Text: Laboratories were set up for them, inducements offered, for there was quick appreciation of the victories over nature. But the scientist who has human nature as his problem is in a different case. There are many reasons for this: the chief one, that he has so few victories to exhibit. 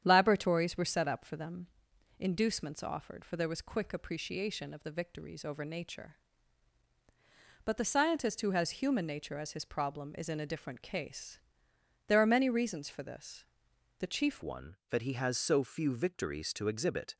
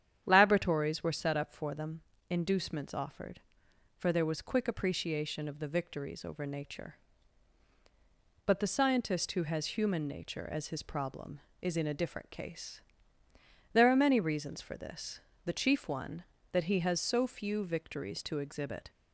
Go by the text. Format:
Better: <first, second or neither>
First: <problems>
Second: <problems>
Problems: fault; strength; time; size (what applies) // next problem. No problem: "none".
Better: second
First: starts louder than the rest; strong; until 1.0 s; 9 dB // changes voice at "one"; from 14.4 s on; 2.7 s long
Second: starts louder than the rest; strong; until 1.2 s; 9.5 dB